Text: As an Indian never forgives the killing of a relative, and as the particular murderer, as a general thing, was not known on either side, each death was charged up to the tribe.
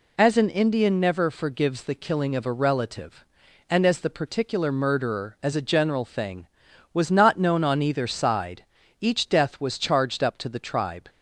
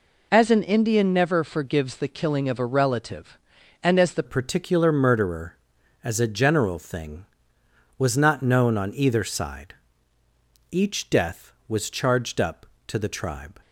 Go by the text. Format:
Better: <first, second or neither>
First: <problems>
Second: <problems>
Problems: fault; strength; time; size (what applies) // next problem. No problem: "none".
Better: first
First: none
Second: changes voice at "particular"; from 4.2 s on; 9.3 s long